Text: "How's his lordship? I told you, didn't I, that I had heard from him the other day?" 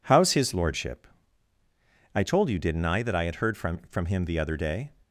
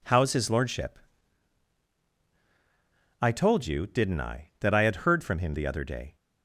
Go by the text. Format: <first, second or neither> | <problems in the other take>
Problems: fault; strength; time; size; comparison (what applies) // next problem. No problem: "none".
second | says "from" twice; at 3.8 s